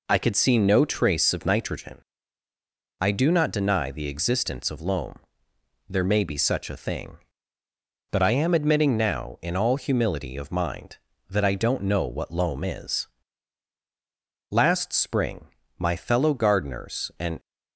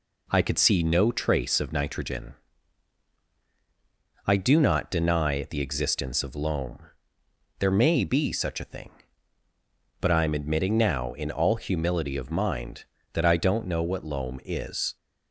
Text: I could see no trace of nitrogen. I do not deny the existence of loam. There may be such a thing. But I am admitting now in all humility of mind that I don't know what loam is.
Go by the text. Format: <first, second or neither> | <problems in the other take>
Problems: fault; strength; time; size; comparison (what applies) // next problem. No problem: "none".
second | goes on to say "Last spring my fellow gardeners and"; strong; from 14.5 s on; 2.8 s long